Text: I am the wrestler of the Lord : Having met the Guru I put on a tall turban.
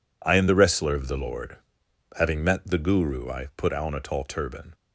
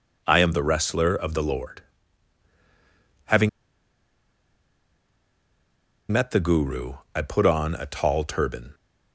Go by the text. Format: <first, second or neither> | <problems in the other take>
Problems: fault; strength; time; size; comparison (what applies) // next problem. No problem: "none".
first | pauses between "Having" and "met"; strong; at 3.4 s; 2.6 s long // pauses between "Guru" and "I"; slight; at 6.9 s; 0.20 s long